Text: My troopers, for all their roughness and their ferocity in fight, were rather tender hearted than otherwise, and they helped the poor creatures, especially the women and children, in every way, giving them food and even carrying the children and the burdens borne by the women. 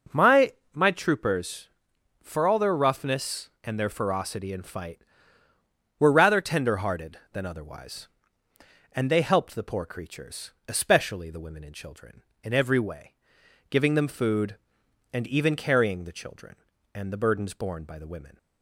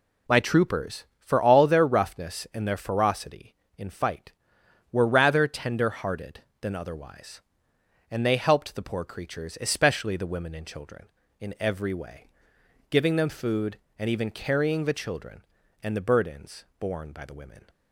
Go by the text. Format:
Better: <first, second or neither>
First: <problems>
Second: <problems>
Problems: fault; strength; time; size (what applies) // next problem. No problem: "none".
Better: second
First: says "My" twice; at 0.7 s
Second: none